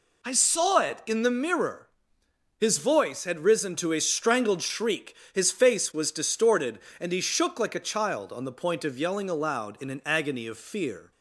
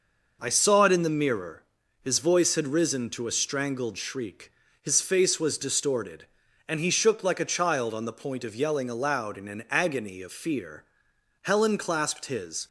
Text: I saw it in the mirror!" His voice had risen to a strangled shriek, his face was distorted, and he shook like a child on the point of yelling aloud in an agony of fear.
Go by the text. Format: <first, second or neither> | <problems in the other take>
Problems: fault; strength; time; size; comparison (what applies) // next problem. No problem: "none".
first | goes on to say "Helen clasped his"; noticeable; from 11.4 s on; 1.2 s long